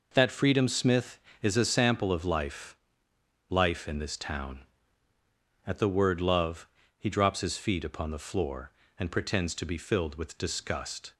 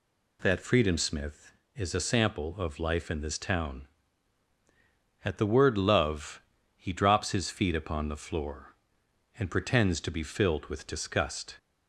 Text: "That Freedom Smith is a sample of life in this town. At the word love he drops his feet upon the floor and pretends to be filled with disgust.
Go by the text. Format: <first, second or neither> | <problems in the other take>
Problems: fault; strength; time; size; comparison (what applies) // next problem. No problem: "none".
second | says "life" twice; at 3.4 s // pauses between "love" and "he"; slight; at 6.6 s; 0.30 s long; slight in the second